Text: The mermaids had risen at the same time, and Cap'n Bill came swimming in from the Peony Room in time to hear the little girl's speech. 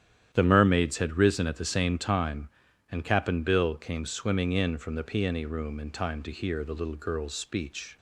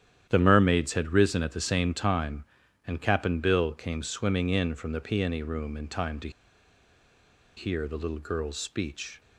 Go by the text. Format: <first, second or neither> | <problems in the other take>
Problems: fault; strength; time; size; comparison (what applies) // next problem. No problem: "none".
first | starts louder than the rest; strong; until 1.3 s; 10.5 dB; strong in the first // pauses between "to" and "hear"; strong; at 6.2 s; 1.2 s long